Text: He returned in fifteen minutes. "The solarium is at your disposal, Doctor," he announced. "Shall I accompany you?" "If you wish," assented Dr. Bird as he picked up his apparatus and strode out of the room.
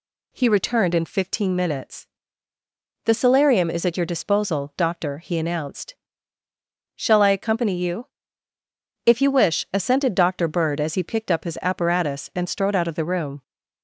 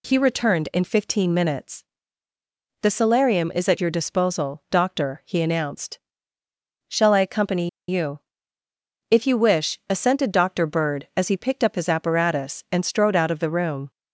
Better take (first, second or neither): first